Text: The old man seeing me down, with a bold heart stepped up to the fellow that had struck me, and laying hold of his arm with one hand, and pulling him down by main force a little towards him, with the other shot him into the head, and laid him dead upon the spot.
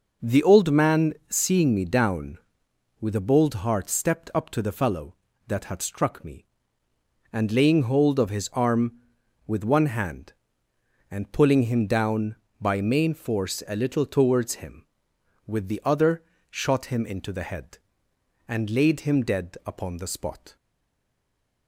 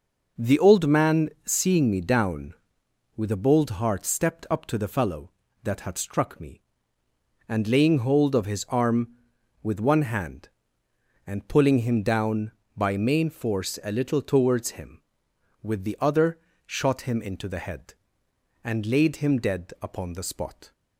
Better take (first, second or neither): second